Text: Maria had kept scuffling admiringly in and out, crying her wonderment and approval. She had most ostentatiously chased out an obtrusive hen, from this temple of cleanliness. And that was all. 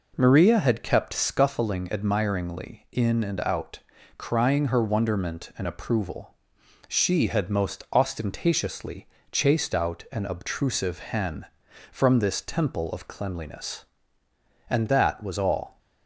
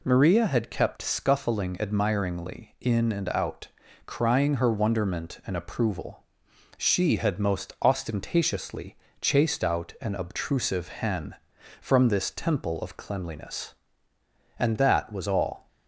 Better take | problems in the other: second | starts louder than the rest; noticeable; until 1.5 s; 4.5 dB // pauses between "ostentatiously" and "chased"; slight; at 9.0 s; 0.24 s long; slight in the second

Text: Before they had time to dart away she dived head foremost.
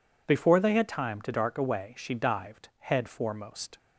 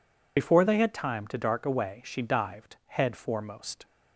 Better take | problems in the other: first | loses the start of "Before"; at 0.3 s; 45 ms

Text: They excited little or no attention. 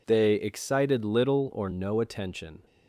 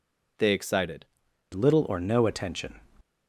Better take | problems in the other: first | changes voice at "little"; from 1.5 s on; 1.2 s long

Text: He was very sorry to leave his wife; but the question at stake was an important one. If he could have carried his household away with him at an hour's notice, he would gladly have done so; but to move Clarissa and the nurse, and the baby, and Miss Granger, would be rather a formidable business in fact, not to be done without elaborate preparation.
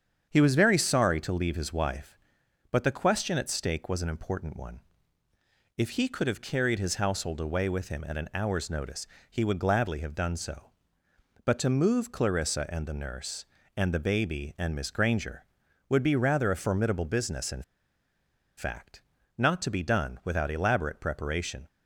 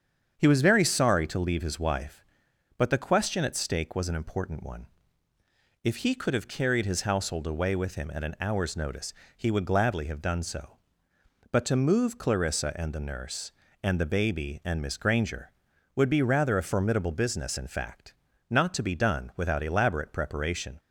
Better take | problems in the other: second | starts louder than the rest; strong; until 1.3 s; 8 dB; strong in the second // pauses between "in" and "fact"; noticeable; at 17.6 s; 0.95 s long

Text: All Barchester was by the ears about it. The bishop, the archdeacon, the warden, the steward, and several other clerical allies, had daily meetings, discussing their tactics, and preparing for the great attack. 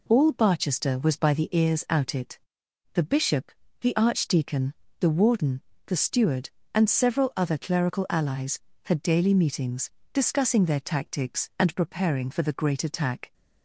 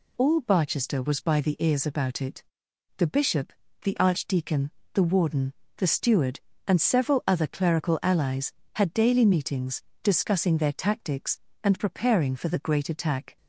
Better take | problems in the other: second | says "out" for "about"; at 1.8 s

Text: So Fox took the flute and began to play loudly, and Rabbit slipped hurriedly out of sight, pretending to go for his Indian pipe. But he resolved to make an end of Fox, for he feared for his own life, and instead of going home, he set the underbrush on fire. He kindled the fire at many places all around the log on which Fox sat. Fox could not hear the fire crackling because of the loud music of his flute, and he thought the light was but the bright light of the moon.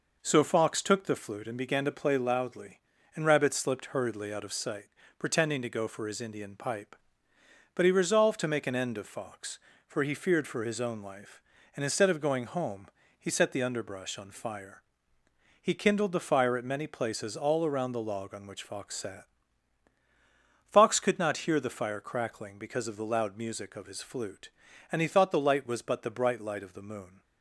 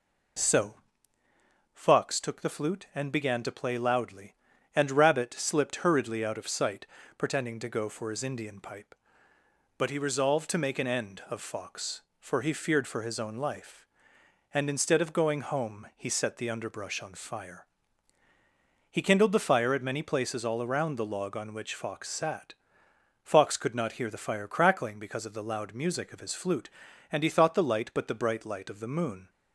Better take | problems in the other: first | pauses between "So" and "Fox"; noticeable; at 0.7 s; 0.98 s long // skips "was"; at 27.9 s

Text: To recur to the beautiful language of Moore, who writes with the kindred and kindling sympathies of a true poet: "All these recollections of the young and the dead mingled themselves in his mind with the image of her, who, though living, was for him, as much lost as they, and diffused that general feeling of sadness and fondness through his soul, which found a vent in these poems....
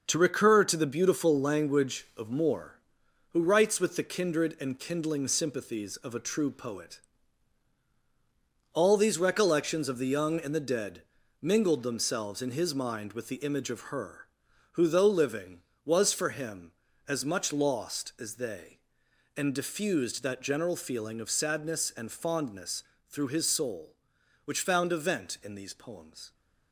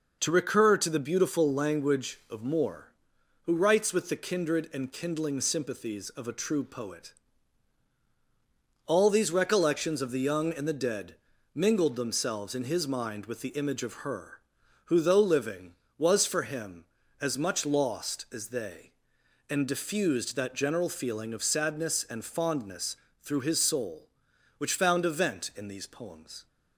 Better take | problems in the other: second | gets quieter; throughout; 7 dB // pauses between "dead" and "mingled"; slight; at 11.0 s; 0.36 s long; slight in the second // pauses between "fondness" and "through"; slight; at 22.8 s; 0.24 s long; slight in the second

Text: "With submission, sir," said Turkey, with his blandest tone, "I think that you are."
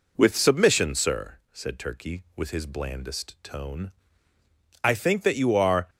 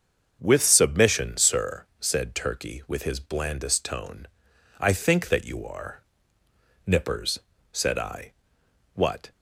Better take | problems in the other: first | starts louder than the rest; until 1.4 s; 6.5 dB // goes on to say "Nippers said I what"; strong; from 6.8 s on; 2.4 s long

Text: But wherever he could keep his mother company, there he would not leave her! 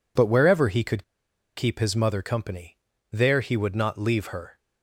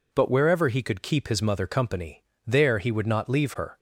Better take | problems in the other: second | pauses between "could" and "keep"; noticeable; at 1.0 s; 0.52 s long

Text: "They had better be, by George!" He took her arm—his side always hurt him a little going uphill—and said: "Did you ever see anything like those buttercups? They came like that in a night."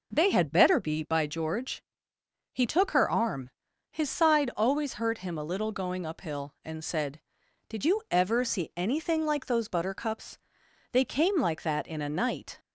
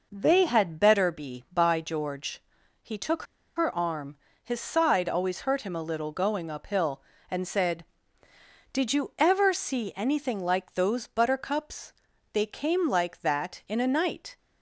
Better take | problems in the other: first | pauses between "took" and "her"; slight; at 3.2 s; 0.33 s long

